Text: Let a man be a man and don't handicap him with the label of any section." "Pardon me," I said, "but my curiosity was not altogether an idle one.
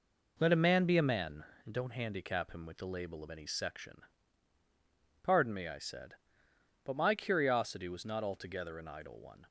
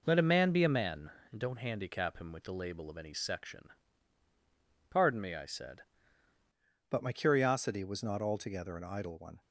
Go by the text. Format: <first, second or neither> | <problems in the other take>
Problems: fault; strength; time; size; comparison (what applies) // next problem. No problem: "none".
first | changes voice at "but"; from 6.9 s on; 2.5 s long